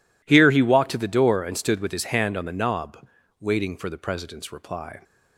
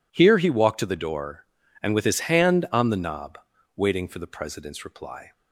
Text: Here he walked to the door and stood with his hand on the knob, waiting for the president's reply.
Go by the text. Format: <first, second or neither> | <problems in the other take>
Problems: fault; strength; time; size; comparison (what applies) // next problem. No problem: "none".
first | skips "stood"; at 1.9 s